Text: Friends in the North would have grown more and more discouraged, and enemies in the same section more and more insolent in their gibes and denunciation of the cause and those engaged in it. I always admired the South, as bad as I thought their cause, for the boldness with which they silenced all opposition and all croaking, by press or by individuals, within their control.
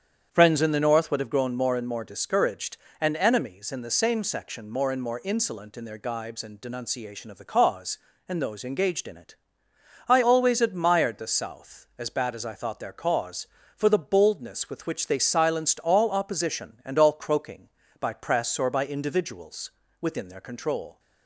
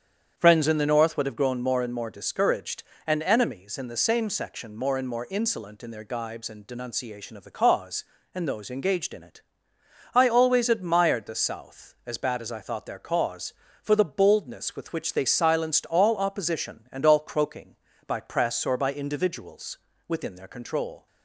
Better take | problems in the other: neither | starts louder than the rest; strong; the same in both

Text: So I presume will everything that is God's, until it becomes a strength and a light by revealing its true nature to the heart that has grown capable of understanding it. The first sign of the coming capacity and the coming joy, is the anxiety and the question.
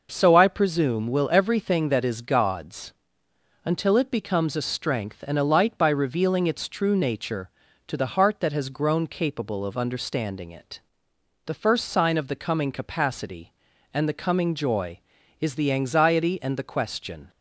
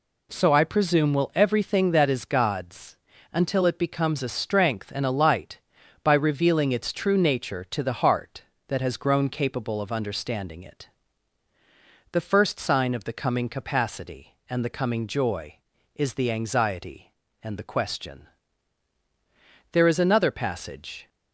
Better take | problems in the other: first | goes on to say "There is another passage"; from 19.7 s on; 1.3 s long

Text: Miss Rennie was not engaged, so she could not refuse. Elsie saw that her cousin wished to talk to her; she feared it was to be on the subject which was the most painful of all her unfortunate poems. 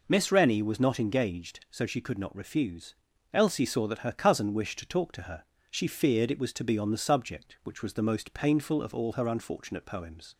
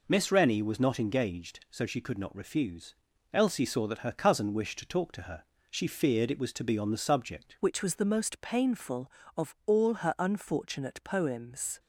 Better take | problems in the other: first | changes voice at "which"; from 7.6 s on; 4.1 s long

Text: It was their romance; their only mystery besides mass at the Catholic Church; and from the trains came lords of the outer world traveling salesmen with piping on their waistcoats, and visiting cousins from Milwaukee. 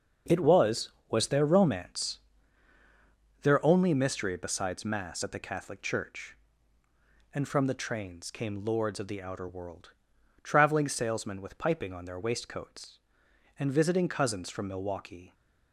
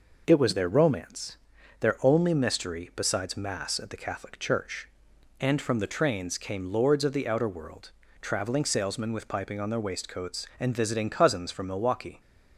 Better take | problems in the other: second | says "was" twice; at 1.0 s // pauses between "world" and "traveling"; noticeable; at 9.9 s; 0.50 s long; slight in the second

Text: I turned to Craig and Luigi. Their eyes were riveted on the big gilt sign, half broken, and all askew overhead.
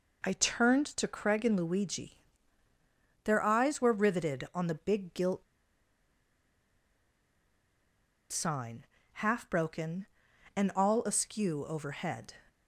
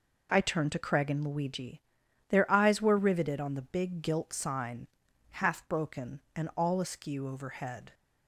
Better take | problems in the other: second | pauses between "gilt" and "sign"; strong; at 5.4 s; 2.8 s long

